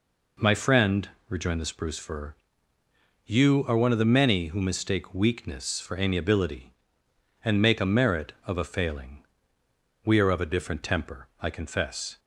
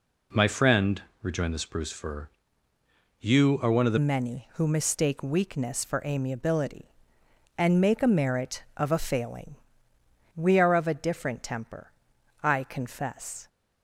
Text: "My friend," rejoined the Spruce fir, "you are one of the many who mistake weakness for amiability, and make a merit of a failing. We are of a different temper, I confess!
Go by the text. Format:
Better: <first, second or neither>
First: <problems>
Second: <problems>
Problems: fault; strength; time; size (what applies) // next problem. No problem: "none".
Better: first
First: none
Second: changes voice at "many"; from 3.9 s on; 9.5 s long